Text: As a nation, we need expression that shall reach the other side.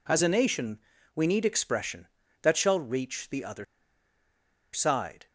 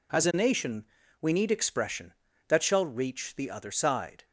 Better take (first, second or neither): second